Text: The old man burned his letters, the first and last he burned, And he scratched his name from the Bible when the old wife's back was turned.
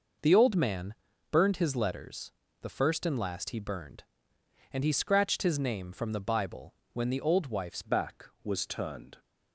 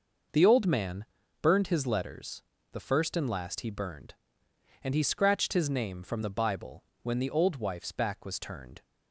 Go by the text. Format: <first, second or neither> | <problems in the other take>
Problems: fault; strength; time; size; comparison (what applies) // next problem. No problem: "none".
second | pauses between "man" and "burned"; slight; at 0.9 s; 0.36 s long; slight in the second // pauses between "Bible" and "when"; slight; at 6.7 s; 0.18 s long; slight in the second // changes voice at "back"; from 7.8 s on; 1.3 s long